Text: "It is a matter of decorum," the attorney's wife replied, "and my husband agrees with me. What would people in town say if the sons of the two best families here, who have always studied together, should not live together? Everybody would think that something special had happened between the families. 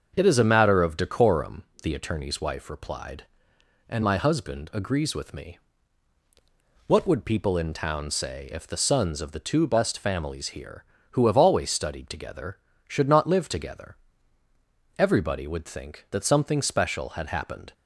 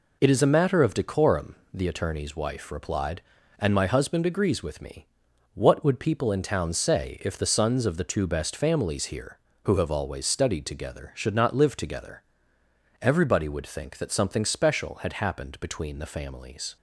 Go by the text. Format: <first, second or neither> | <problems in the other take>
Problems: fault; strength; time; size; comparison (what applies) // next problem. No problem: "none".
second | starts louder than the rest; until 1.1 s; 6.5 dB // stops before "between the families"; at 17.7 s